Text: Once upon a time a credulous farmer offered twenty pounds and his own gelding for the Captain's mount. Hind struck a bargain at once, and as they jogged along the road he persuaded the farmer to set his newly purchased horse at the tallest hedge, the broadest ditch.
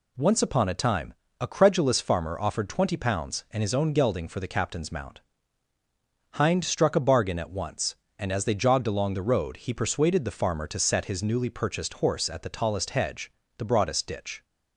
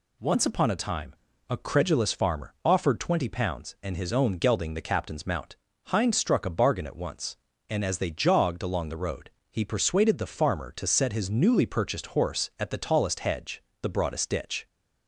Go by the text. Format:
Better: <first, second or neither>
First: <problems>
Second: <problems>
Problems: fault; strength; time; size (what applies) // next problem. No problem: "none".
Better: first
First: pauses between "time" and "a"; slight; at 1.1 s; 0.28 s long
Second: pauses between "time" and "a"; slight; at 1.1 s; 0.36 s long // skips "for"; at 4.7 s // pauses between "road" and "he"; slight; at 9.2 s; 0.22 s long